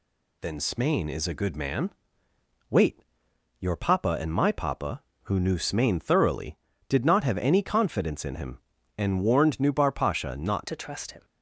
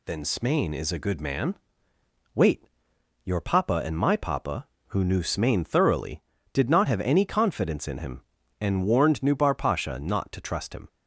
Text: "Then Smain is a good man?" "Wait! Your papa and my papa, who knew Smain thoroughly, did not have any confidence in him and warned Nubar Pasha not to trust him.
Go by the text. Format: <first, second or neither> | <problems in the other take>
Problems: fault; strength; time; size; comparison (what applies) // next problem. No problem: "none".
second | changes voice at "to"; from 10.6 s on; 0.6 s long